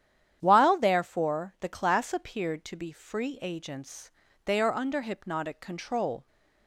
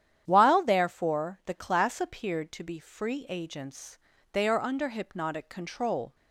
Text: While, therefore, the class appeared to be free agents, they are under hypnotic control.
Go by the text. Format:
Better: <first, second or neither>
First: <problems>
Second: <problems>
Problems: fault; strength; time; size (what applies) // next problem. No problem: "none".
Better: neither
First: starts louder than the rest; strong; until 1.4 s; 10 dB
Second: starts louder than the rest; strong; until 1.2 s; 10 dB